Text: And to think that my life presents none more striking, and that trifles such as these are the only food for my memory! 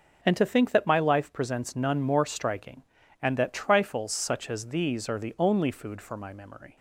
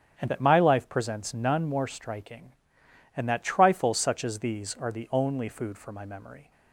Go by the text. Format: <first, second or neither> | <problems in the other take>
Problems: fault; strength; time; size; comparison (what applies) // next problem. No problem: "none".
first | starts louder than the rest; strong; until 1.2 s; 9 dB // skips "to think"; at 0.2 s